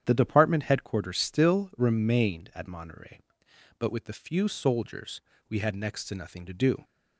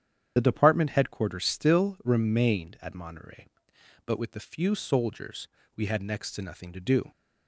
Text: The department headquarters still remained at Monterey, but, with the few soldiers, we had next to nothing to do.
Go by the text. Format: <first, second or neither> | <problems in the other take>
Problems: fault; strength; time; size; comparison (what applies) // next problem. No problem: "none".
first | loses the start of "The"; at 0.3 s; 40 ms // starts louder than the rest; strong; until 1.3 s; 9 dB; strong in the first